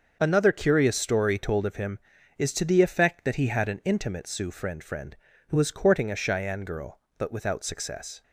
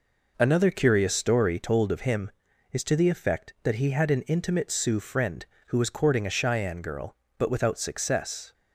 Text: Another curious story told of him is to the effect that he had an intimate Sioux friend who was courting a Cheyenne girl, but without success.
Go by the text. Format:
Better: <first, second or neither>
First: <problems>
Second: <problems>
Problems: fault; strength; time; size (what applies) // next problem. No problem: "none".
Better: second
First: starts louder than the rest; until 1.2 s; 6.5 dB // says "friend" twice; at 4.8 s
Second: none